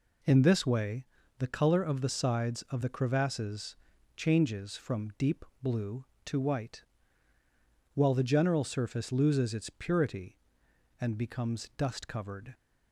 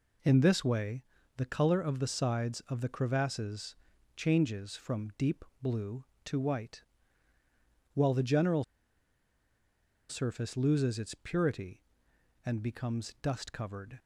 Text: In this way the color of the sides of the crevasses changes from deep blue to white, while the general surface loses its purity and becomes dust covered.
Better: first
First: pauses between "way" and "the"; slight; at 1.0 s; 0.36 s long // pauses between "crevasses" and "changes"; at 3.7 s; 0.40 s long // pauses between "deep" and "blue"; slight; at 5.4 s; 0.16 s long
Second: pauses between "way" and "the"; slight; at 1.0 s; 0.36 s long // pauses between "crevasses" and "changes"; at 3.7 s; 0.40 s long // pauses between "deep" and "blue"; slight; at 5.4 s; 0.16 s long // pauses between "general" and "surface"; strong; at 8.6 s; 1.4 s long

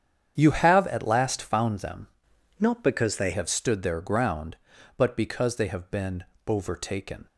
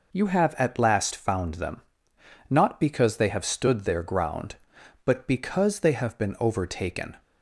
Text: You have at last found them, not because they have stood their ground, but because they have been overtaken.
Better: second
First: starts louder than the rest; strong; until 1.4 s; 8.5 dB // changes voice from "not" to "they"; from 2.5 to 3.3 s; 0.8 s long // pauses between "been" and "overtaken"; slight; at 6.2 s; 0.22 s long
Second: none

